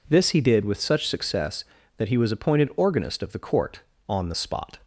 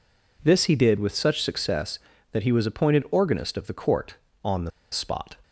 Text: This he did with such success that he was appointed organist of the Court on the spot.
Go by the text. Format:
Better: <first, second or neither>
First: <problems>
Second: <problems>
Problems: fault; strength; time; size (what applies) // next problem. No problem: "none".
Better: first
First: none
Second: pauses between "the" and "spot"; slight; at 4.6 s; 0.21 s long